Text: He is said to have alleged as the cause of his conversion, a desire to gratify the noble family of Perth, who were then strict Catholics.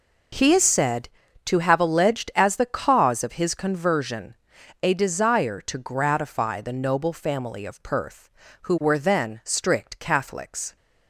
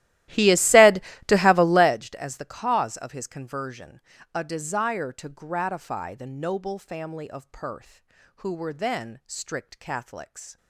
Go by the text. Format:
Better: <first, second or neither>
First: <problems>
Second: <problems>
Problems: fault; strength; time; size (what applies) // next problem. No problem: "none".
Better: first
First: none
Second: starts louder than the rest; strong; until 2.0 s; 15 dB